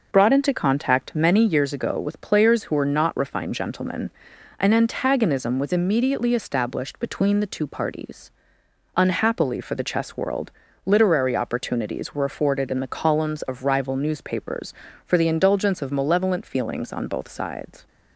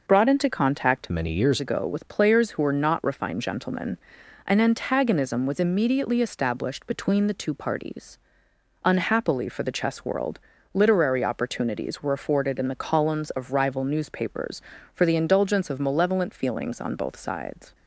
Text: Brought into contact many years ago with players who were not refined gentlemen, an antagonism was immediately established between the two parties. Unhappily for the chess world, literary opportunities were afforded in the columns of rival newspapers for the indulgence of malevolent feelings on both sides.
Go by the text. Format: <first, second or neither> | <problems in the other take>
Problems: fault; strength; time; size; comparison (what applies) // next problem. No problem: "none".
first | changes voice from "many" to "years"; from 1.0 to 1.5 s; 0.5 s long